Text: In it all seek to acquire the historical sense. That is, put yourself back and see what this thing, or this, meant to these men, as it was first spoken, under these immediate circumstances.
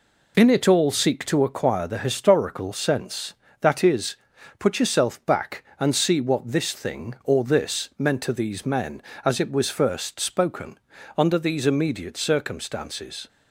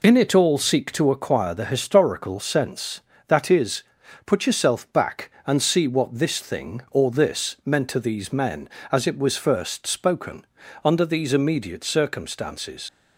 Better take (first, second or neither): first